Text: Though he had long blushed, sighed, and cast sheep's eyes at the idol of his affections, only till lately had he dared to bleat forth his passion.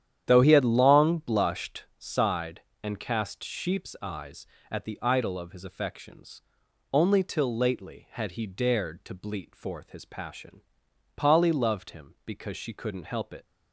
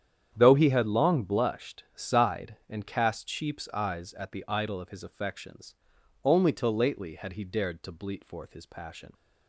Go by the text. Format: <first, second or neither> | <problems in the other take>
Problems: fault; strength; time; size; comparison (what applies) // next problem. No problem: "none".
second | starts louder than the rest; strong; until 1.2 s; 10 dB; strong in the second // goes on to say "Polly loved him because she couldn't help it"; strong; from 11.1 s on; 2.3 s long